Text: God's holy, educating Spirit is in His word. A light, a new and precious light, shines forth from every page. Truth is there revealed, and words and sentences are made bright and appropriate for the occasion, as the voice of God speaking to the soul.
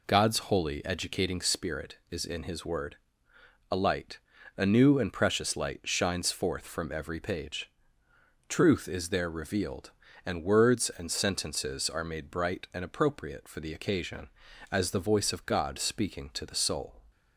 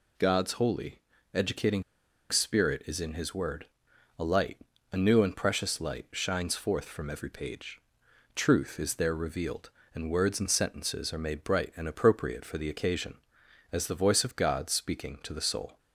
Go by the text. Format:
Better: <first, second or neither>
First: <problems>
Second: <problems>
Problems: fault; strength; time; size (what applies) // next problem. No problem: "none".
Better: first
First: none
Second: pauses between "educating" and "Spirit"; noticeable; at 1.8 s; 0.47 s long